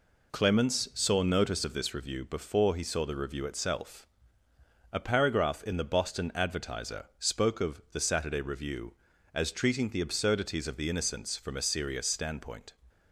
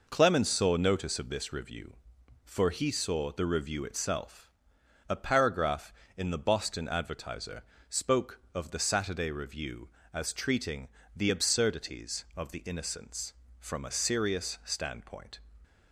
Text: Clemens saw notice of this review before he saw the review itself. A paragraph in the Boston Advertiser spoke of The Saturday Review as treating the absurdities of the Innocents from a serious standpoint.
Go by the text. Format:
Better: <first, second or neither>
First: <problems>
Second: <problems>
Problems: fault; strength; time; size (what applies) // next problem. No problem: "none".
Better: first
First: none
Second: says "for" for "before"; at 2.4 s // pauses between "Advertiser" and "spoke"; slight; at 7.6 s; 0.28 s long // pauses between "treating" and "the"; slight; at 10.8 s; 0.28 s long